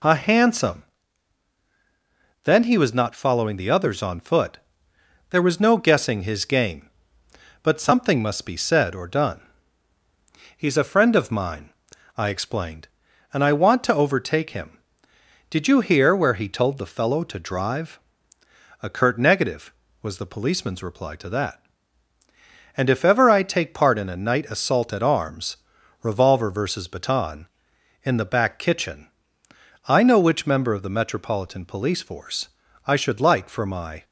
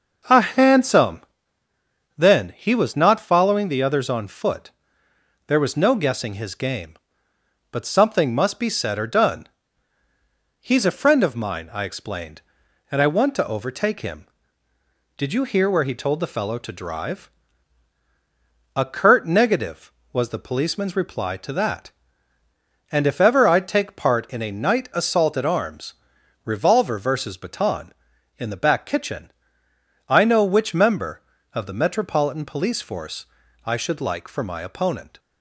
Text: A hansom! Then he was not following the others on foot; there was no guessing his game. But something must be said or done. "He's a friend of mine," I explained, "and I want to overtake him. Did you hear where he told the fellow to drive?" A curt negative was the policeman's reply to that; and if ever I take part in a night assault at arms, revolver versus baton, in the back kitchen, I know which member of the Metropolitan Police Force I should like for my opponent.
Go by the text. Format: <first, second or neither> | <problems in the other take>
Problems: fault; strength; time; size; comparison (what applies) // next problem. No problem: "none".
second | pauses between "Force" and "I"; slight; at 32.4 s; 0.36 s long; also in the second // stops before "opponent"; at 34.0 s